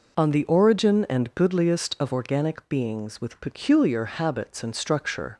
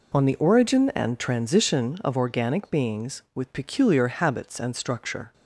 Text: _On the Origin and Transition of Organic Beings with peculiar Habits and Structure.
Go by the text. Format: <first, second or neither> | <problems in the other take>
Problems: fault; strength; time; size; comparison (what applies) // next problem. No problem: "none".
second | says "Goodliest" for "Transition"; at 1.3 s